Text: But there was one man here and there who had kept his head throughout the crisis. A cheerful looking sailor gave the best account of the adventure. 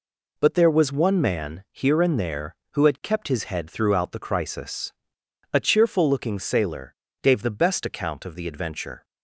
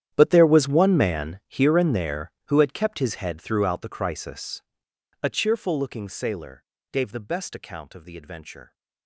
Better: first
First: pauses between "sailor" and "gave"; slight; at 6.9 s; 0.28 s long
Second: gets quieter; strong; throughout; 18 dB // pauses between "sailor" and "gave"; slight; at 6.6 s; 0.28 s long

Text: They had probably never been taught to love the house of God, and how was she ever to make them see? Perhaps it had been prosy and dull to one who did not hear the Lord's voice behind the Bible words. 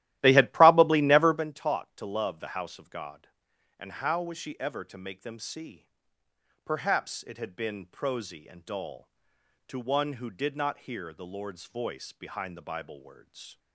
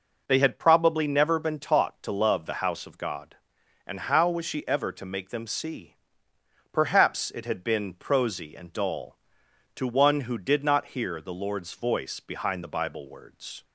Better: second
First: starts louder than the rest; strong; until 1.5 s; 14.5 dB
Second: none

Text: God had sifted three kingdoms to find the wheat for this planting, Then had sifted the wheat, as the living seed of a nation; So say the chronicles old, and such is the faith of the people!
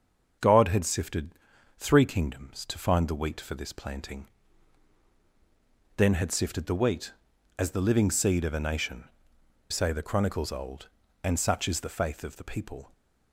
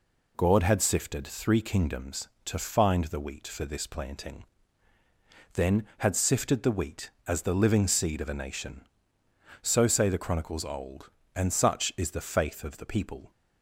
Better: second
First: starts louder than the rest; until 1.8 s; 6.5 dB // pauses between "sifted" and "three"; at 1.3 s; 0.44 s long // skips "So"; at 9.3 s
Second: none

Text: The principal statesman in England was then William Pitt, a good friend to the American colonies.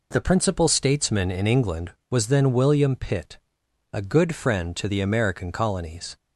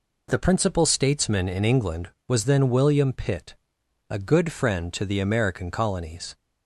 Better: neither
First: none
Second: none

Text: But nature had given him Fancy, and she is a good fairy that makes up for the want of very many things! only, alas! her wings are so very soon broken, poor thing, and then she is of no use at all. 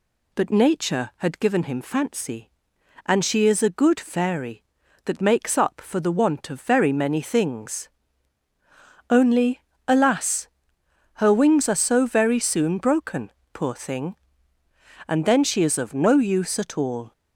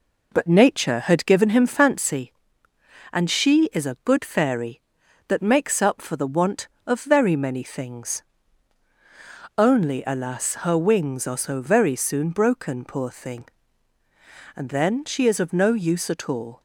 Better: first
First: none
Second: starts louder than the rest; noticeable; until 2.2 s; 4 dB

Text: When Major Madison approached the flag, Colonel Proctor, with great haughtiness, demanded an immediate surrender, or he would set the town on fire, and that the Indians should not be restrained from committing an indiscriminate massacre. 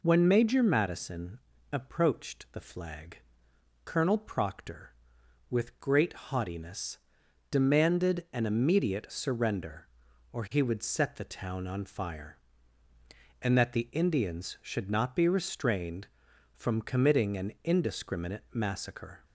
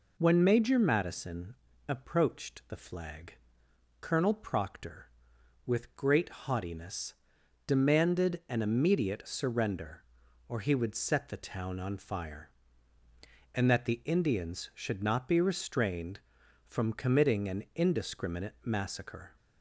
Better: neither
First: pauses between "Madison" and "approached"; slight; at 1.3 s; 0.34 s long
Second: pauses between "Madison" and "approached"; slight; at 1.5 s; 0.34 s long

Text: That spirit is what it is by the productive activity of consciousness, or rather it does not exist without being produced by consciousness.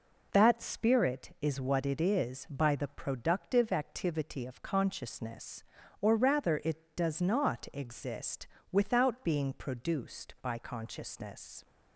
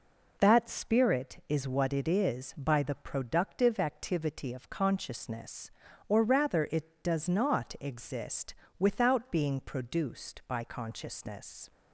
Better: neither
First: pauses between "exist" and "without"; slight; at 8.4 s; 0.24 s long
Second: pauses between "exist" and "without"; slight; at 8.5 s; 0.24 s long

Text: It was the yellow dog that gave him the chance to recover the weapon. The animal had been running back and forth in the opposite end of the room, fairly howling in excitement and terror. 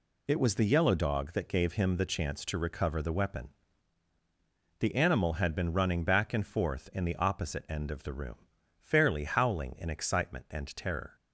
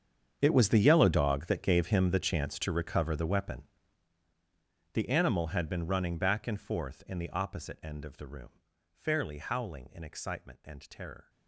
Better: first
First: none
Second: gets quieter; strong; throughout; 18 dB

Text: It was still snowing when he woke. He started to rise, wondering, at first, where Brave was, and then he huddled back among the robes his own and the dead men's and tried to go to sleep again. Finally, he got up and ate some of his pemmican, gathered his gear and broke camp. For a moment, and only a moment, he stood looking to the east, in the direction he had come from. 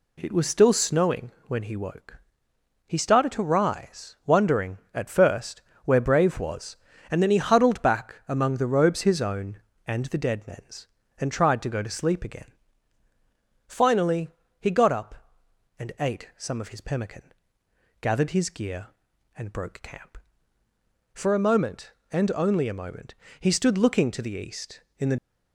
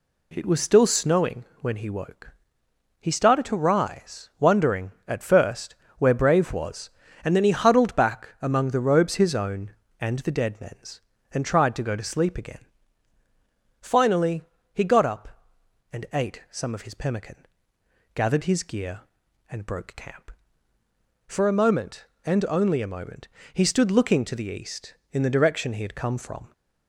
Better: second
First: pauses between "snowing" and "when"; slight; at 1.3 s; 0.16 s long // stops before "direction he had come from"; at 25.1 s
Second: pauses between "snowing" and "when"; slight; at 1.4 s; 0.16 s long

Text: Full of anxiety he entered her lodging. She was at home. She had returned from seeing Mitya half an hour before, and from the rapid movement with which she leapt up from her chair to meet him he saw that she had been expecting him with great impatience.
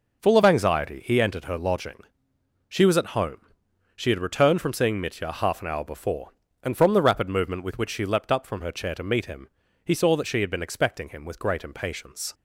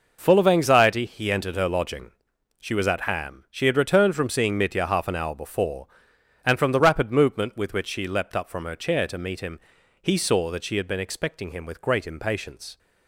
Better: first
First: pauses between "him" and "he"; at 9.4 s; 0.38 s long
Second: says "ham" for "home"; at 3.0 s // pauses between "him" and "he"; at 9.6 s; 0.42 s long

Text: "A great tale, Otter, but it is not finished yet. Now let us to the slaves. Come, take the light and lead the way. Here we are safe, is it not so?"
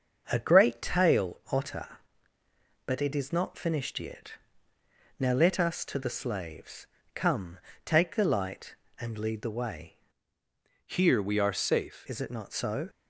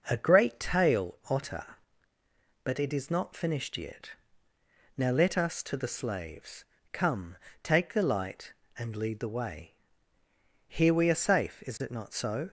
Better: second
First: starts louder than the rest; until 1.3 s; 6.5 dB // changes voice from "Here" to "safe"; from 10.8 to 12.0 s; 1.2 s long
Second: none

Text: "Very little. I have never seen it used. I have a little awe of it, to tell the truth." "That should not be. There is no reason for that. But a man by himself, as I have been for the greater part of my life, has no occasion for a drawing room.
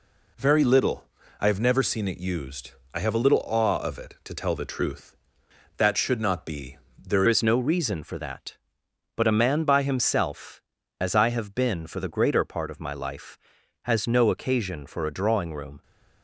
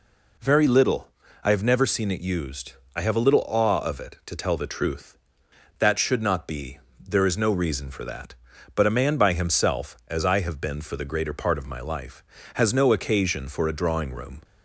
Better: second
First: changes voice at "is"; from 7.2 s on; 8.6 s long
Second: none

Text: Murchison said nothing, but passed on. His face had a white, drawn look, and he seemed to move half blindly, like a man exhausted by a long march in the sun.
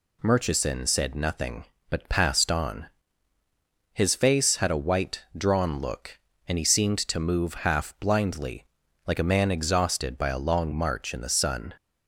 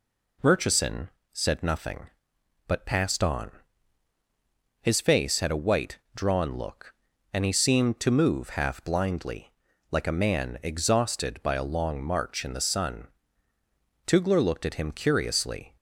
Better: first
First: none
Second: pauses between "Murchison" and "said"; slight; at 1.0 s; 0.24 s long // goes on to say "Tugler looked at him curiously"; strong; from 14.0 s on; 1.6 s long

